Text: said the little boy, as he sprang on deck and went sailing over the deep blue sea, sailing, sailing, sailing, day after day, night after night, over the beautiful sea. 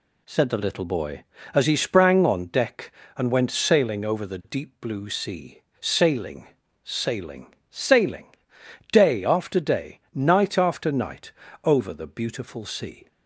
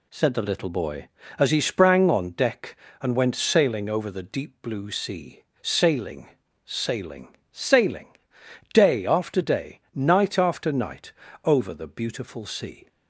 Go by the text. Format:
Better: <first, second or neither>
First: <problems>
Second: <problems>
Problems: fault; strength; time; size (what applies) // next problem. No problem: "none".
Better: neither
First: none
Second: none